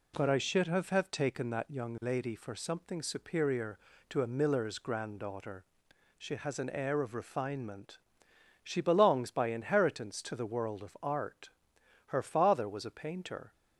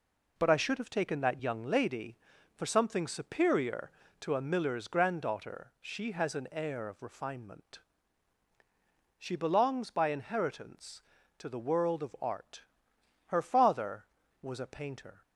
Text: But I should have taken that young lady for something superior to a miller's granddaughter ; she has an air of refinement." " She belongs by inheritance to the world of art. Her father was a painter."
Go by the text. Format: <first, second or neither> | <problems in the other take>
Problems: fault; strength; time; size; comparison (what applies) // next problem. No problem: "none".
second | says "have" twice; at 0.9 s